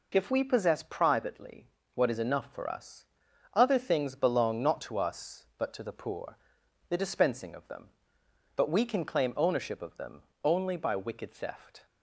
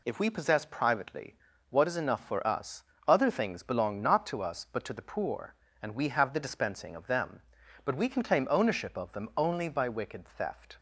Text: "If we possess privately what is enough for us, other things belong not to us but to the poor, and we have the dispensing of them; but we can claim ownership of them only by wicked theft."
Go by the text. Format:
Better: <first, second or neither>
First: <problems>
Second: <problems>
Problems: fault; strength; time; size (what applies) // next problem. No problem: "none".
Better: second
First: pauses between "privately" and "what"; slight; at 1.7 s; 0.24 s long // skips "and we have"; at 6.6 s // pauses between "them" and "only"; slight; at 10.2 s; 0.22 s long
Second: pauses between "privately" and "what"; slight; at 1.3 s; 0.34 s long